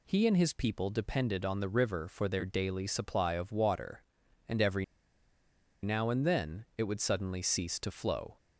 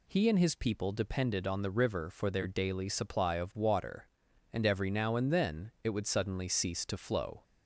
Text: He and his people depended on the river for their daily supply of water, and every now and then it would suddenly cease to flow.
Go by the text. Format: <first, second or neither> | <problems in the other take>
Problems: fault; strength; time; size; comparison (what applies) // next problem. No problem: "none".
second | pauses between "every" and "now"; at 4.8 s; 0.98 s long